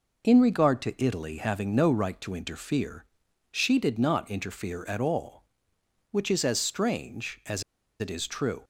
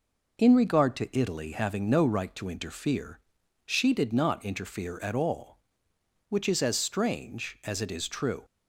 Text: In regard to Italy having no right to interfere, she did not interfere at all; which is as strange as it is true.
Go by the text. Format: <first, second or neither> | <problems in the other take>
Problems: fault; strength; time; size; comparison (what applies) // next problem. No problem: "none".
second | pauses between "as" and "it"; at 7.6 s; 0.37 s long